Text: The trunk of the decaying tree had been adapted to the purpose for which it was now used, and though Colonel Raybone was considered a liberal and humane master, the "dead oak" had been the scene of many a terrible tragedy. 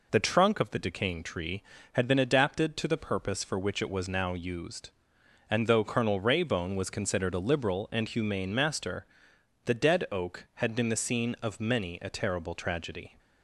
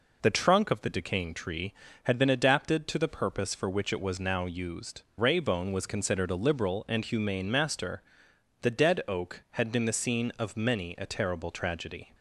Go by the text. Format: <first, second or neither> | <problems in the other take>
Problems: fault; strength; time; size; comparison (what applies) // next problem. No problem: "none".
first | skips "and though Colonel"; at 5.0 s